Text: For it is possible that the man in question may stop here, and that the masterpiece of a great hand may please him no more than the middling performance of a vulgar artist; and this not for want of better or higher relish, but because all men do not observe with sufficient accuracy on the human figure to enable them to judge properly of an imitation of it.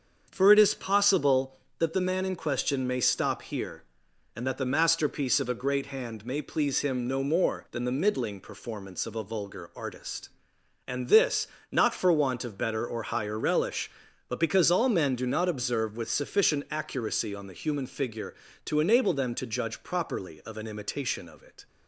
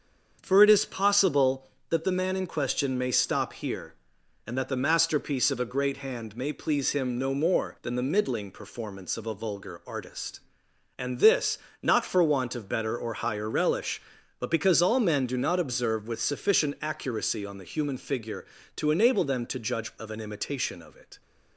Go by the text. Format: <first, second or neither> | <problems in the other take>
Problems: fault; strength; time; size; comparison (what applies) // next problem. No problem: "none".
first | starts louder than the rest; until 1.4 s; 7 dB; also in the first // pauses between "this" and "not"; slight; at 11.5 s; 0.24 s long; slight in the first // skips "properly"; at 19.9 s